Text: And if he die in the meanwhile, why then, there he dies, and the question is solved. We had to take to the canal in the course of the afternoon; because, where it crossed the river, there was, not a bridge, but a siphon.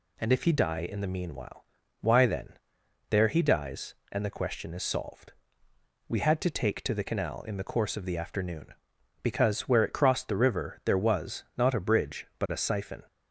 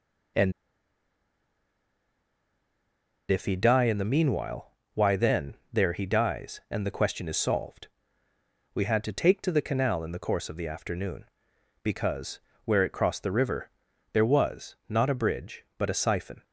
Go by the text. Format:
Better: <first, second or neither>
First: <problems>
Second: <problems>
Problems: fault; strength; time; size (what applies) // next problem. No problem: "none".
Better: first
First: none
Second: pauses between "And" and "if"; strong; at 0.5 s; 2.7 s long